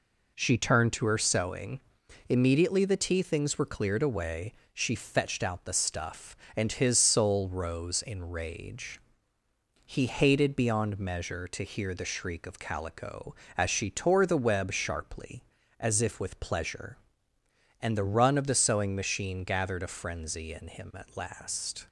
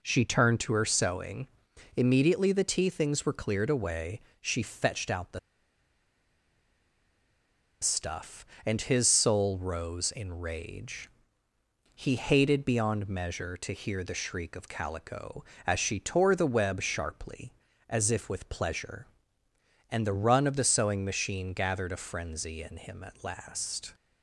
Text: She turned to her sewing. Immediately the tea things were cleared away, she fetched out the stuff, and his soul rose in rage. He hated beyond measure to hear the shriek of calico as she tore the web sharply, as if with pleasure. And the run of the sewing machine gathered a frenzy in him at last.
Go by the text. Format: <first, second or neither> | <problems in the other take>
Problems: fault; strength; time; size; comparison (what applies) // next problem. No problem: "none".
first | pauses between "the" and "stuff"; strong; at 5.3 s; 2.4 s long